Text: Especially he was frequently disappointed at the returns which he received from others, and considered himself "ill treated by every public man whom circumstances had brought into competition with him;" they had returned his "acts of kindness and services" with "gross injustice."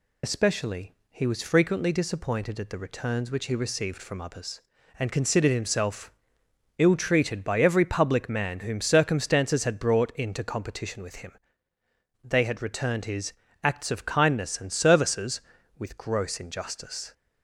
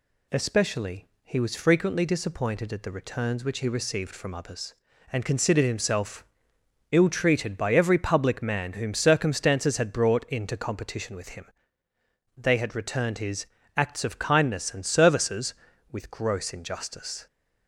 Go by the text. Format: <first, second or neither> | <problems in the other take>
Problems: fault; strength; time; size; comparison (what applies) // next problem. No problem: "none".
second | loses the start of "Especially"; at 0.2 s; 65 ms // pauses between "Especially" and "he"; slight; at 0.9 s; 0.18 s long; slight in the second // pauses between "himself" and "ill"; noticeable; at 6.1 s; 0.66 s long; noticeable in the second // pauses between "his" and "acts"; slight; at 13.3 s; 0.28 s long; slight in the second